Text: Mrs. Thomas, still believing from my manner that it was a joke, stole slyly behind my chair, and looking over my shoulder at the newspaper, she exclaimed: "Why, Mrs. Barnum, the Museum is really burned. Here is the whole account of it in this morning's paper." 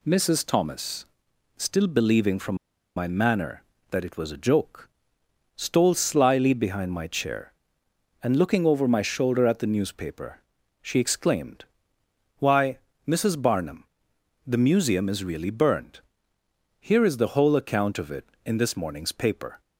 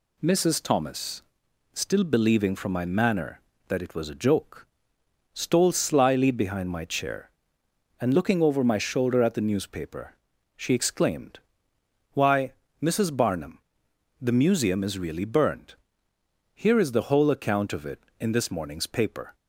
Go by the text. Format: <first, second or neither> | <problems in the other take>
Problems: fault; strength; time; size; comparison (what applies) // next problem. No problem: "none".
second | pauses between "from" and "my"; at 2.5 s; 0.41 s long